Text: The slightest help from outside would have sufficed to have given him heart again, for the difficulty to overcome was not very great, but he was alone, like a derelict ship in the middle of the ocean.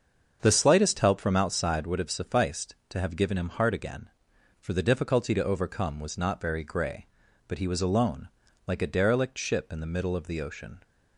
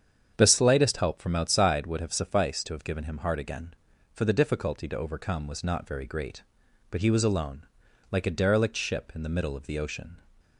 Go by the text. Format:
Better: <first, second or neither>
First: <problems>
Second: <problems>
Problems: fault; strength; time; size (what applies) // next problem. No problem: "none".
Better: second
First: starts louder than the rest; until 1.4 s; 7 dB // says "grey" for "great"; at 6.6 s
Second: starts louder than the rest; strong; until 1.3 s; 8 dB